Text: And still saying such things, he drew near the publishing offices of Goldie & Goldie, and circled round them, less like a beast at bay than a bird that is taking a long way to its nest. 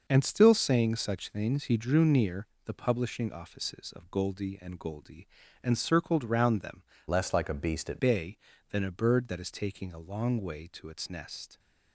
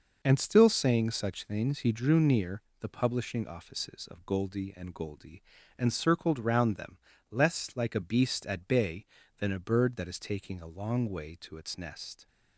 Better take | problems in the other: second | pauses between "near" and "the"; slight; at 2.4 s; 0.18 s long; slight in the second // changes voice from "less" to "at"; from 7.0 to 7.9 s; 0.9 s long

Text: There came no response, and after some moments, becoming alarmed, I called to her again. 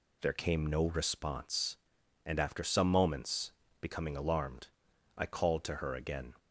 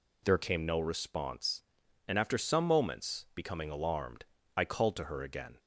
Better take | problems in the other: neither | none

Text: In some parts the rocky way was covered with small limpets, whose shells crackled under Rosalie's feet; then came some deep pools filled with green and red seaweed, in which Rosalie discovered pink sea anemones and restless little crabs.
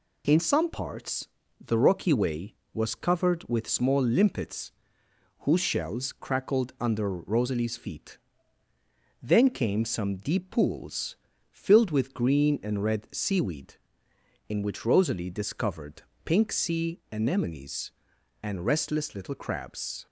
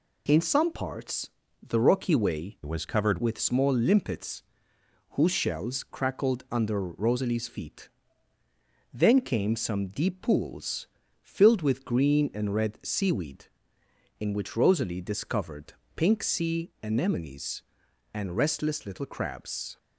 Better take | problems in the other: first | pauses between "parts" and "the"; slight; at 1.2 s; 0.34 s long; slight in the first // changes voice from "was" to "covered"; from 2.6 to 3.1 s; 0.5 s long // pauses between "pools" and "filled"; slight; at 10.8 s; 0.36 s long; slight in the first // pauses between "discovered" and "pink"; slight; at 15.7 s; 0.20 s long; slight in the first

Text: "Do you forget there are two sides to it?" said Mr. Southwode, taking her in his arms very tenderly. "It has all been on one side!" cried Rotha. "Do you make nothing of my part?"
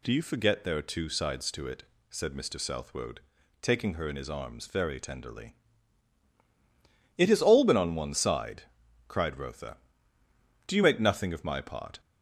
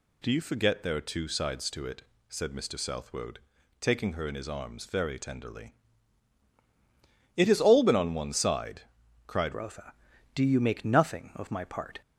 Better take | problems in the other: first | changes voice at "Rotha"; from 9.5 s on; 2.5 s long

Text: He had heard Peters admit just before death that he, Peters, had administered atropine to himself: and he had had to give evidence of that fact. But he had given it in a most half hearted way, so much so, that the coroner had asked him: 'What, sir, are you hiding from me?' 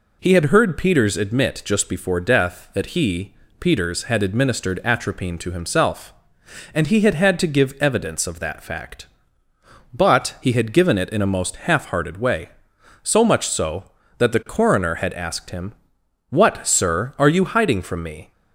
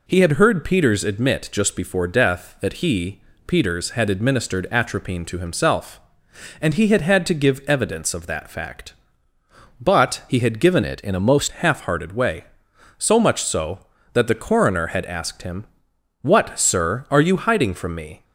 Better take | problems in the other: first | changes voice from "it" to "most"; from 10.8 to 11.4 s; 0.6 s long

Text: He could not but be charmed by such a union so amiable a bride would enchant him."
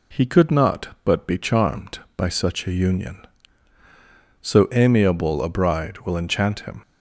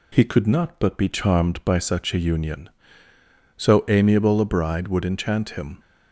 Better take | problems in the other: second | says "will" for "would"; at 5.9 s

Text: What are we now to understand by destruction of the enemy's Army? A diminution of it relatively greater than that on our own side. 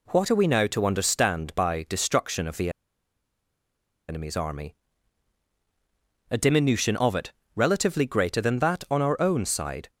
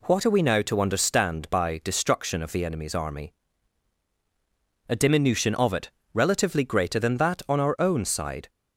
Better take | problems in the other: second | pauses between "the" and "enemy's"; strong; at 2.7 s; 1.3 s long // pauses between "it" and "relatively"; slight; at 7.3 s; 0.22 s long; slight in the second

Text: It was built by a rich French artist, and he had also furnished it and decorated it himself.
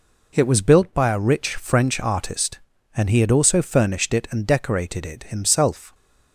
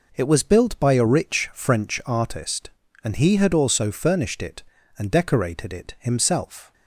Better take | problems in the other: neither | none

